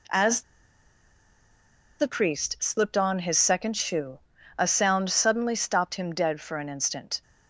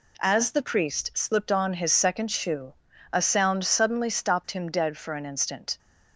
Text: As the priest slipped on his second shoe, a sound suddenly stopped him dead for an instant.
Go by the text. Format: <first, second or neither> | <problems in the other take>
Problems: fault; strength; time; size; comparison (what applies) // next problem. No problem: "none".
second | pauses between "As" and "the"; strong; at 0.4 s; 1.5 s long